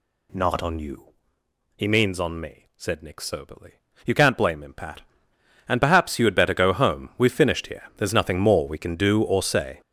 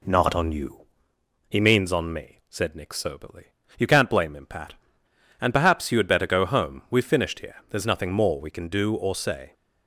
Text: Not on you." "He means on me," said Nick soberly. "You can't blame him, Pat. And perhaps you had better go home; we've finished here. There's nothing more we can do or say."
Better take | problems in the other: second | gets louder; strong; throughout; 11 dB

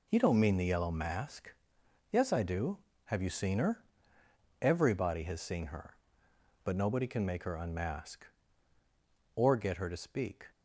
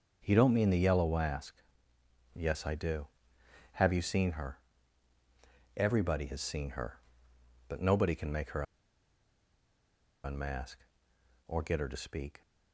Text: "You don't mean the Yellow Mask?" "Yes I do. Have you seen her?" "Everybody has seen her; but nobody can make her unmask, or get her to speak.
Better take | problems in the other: first | starts louder than the rest; noticeable; until 1.3 s; 6 dB // pauses between "her" and "unmask"; strong; at 8.6 s; 1.6 s long

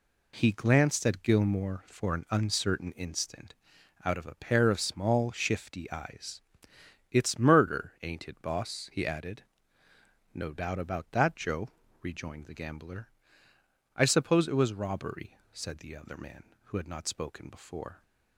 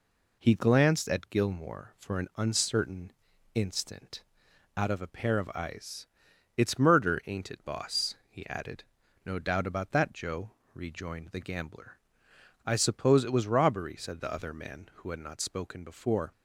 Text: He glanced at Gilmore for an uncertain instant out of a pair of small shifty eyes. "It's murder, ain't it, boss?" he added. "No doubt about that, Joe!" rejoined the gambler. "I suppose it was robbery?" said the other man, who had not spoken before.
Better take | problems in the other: first | pauses between "uncertain" and "instant"; at 3.1 s; 0.42 s long // pauses between "instant" and "out"; noticeable; at 4.2 s; 0.54 s long; noticeable in the first // skips "small shifty"; at 5.5 s

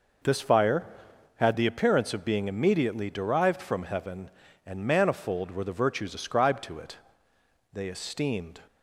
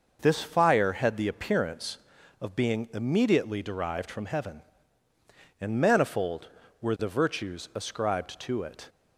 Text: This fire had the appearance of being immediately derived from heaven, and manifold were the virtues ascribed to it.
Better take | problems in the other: second | goes on to say "They esteemed"; noticeable; from 7.7 s on; 0.88 s long

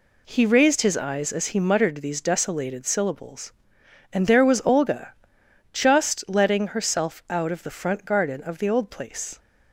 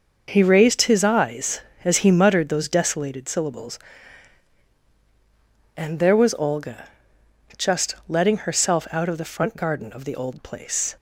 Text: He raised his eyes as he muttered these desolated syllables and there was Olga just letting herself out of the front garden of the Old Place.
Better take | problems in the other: first | starts louder than the rest; noticeable; until 1.2 s; 6 dB // says "those" for "these"; at 2.4 s // pauses between "Olga" and "just"; noticeable; at 6.8 s; 0.70 s long; noticeable in the first

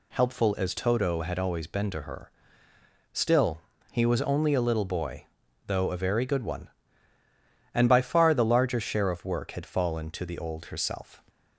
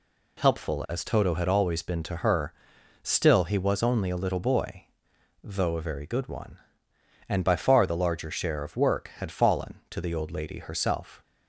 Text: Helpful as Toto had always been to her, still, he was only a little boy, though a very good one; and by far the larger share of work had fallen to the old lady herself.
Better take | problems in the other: second | skips "lady"; at 10.6 s

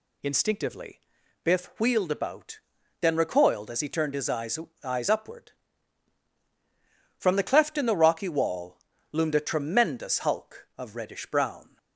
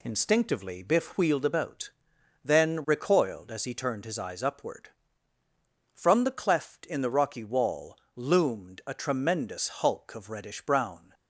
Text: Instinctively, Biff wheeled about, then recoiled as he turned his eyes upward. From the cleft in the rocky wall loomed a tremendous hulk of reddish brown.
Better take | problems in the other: second | says "eyes" twice; at 4.8 s // pauses between "wall" and "loomed"; slight; at 8.7 s; 0.34 s long; slight in the second

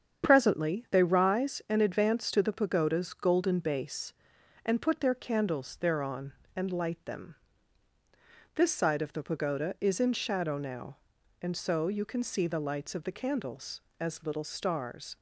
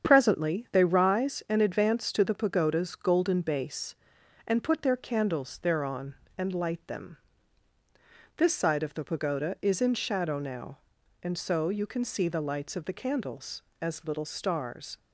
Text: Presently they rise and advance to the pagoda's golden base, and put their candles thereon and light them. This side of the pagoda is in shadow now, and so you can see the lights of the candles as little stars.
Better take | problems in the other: neither | starts louder than the rest; strong; the same in both

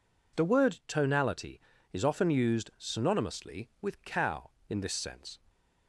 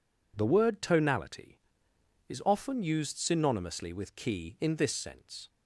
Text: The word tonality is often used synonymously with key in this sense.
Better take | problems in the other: second | says "cow" for "key"; at 4.0 s

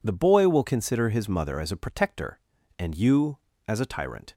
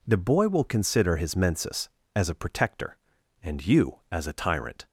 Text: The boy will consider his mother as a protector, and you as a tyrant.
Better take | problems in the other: first | says "mensis" for "mother"; at 1.3 s

